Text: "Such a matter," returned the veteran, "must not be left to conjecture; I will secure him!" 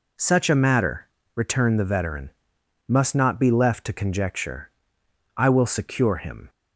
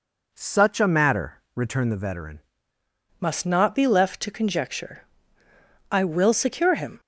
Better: first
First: none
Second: changes voice at "must"; from 3.1 s on; 3.8 s long

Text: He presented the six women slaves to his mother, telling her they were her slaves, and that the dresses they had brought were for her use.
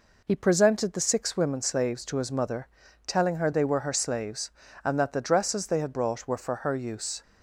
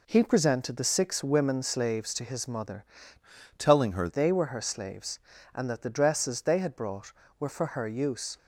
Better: first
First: none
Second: changes voice from "telling" to "her"; from 3.5 to 4.0 s; 0.5 s long

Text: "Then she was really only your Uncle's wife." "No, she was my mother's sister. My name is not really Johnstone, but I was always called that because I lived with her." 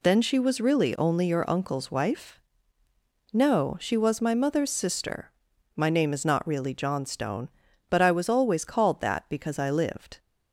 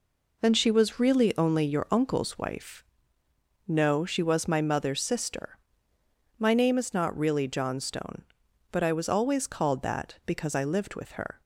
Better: second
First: stops before "with her"; at 10.1 s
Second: none

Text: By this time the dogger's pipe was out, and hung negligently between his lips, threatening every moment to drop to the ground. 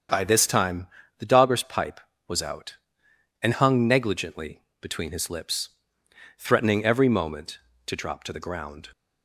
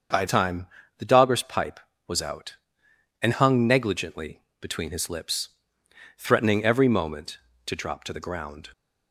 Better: first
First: starts louder than the rest; strong; until 1.4 s; 7.5 dB // pauses between "time" and "the"; slight; at 0.8 s; 0.30 s long // pauses between "negligently" and "between"; slight; at 4.6 s; 0.20 s long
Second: starts louder than the rest; until 1.4 s; 7 dB // skips "this"; at 0.2 s // pauses between "time" and "the"; slight; at 0.6 s; 0.30 s long // pauses between "negligently" and "between"; slight; at 4.3 s; 0.20 s long

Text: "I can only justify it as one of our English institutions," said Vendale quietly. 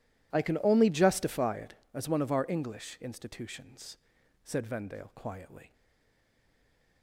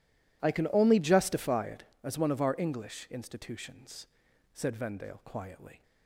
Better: second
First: stays silent after the last word; noticeable; from 5.7 s on; 1.3 s long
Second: none

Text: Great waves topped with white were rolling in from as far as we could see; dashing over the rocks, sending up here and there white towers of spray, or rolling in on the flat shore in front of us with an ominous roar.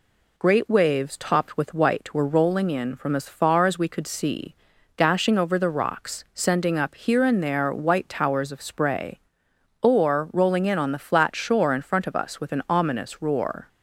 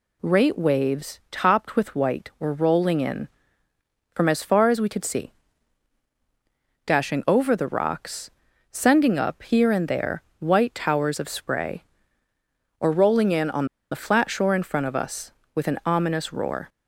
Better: first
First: none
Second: pauses between "there" and "white"; slight; at 10.2 s; 0.18 s long // pauses between "on" and "the"; slight; at 13.6 s; 0.26 s long

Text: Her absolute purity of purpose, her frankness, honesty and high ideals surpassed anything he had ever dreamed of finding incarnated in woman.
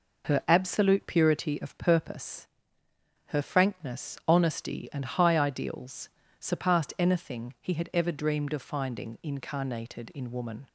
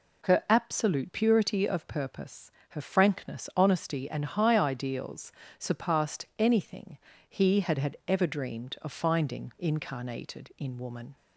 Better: first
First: pauses between "ideals" and "surpassed"; slight; at 6.0 s; 0.30 s long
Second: pauses between "ideals" and "surpassed"; slight; at 5.3 s; 0.26 s long // pauses between "anything" and "he"; slight; at 6.9 s; 0.30 s long // says "had" twice; at 7.7 s

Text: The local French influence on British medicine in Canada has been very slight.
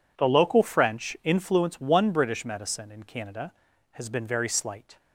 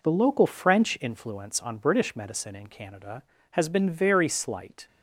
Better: second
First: says "one" for "on"; at 1.7 s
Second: none

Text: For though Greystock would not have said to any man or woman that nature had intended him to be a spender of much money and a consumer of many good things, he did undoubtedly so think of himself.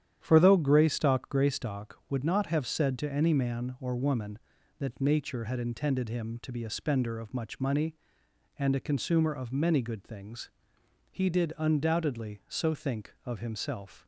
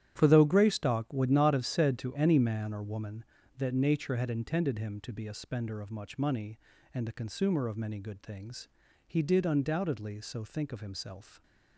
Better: second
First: starts louder than the rest; strong; until 1.2 s; 10 dB // says "Greystock" twice; at 1.2 s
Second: starts louder than the rest; strong; until 1.1 s; 11 dB

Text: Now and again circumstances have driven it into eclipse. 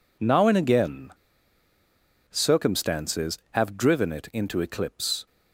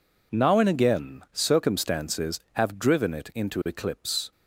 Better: second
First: pauses between "again" and "circumstances"; at 1.0 s; 1.2 s long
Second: none

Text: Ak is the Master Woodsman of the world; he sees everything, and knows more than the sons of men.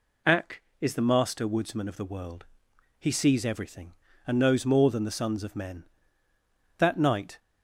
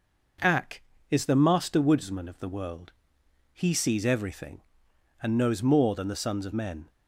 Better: second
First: goes on to say "That night"; from 6.7 s on; 0.60 s long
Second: none

